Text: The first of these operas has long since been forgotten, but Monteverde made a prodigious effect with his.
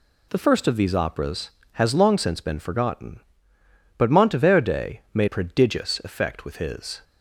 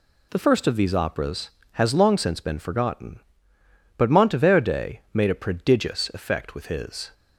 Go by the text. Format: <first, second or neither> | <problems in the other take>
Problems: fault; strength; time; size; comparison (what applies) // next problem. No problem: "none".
second | skips "a"; at 5.2 s